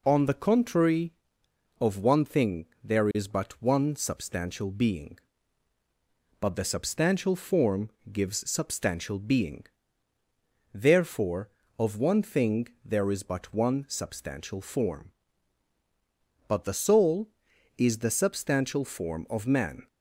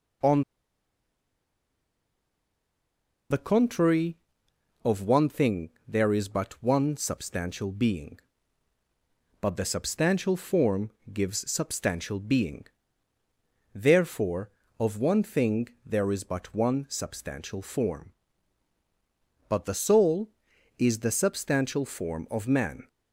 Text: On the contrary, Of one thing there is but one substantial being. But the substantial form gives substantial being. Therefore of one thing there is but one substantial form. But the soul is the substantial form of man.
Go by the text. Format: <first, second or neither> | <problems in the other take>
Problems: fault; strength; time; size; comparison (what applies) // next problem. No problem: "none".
first | pauses between "On" and "the"; strong; at 0.4 s; 2.8 s long // pauses between "thing" and "there"; slight; at 5.6 s; 0.18 s long; slight in the first // pauses between "form" and "gives"; slight; at 10.8 s; 0.22 s long; slight in the first